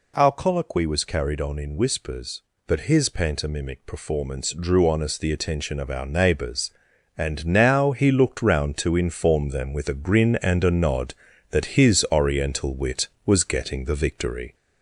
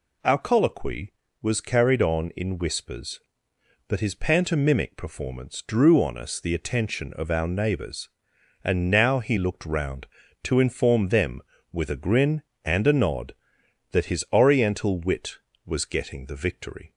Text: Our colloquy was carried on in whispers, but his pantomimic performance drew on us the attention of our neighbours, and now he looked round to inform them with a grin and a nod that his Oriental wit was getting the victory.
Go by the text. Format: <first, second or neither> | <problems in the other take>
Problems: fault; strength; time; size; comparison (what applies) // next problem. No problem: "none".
second | gets louder; slight; throughout; 2.5 dB